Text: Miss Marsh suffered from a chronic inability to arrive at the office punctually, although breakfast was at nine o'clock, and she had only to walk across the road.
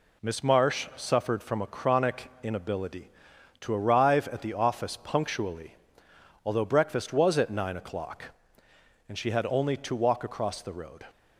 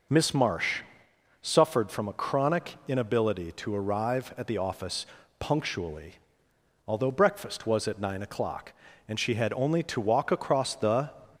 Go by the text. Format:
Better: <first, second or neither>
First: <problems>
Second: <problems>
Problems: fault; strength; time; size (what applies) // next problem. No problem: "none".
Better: first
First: none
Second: pauses between "Marsh" and "suffered"; noticeable; at 0.8 s; 0.62 s long // pauses between "office" and "punctually"; slight; at 5.0 s; 0.34 s long // stops before "road"; at 11.3 s